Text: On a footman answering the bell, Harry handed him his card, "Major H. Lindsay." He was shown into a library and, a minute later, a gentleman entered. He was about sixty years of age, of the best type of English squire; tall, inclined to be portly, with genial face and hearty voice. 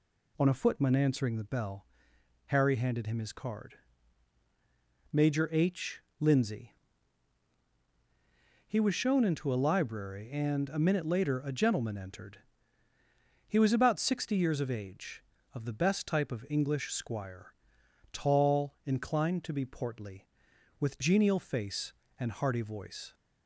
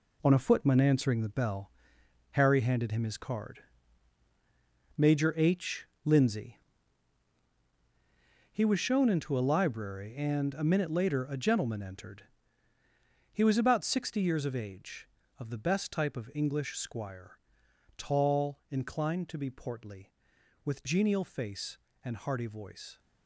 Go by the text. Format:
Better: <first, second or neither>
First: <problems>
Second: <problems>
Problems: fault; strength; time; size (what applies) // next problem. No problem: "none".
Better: first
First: none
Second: gets quieter; strong; throughout; 8.5 dB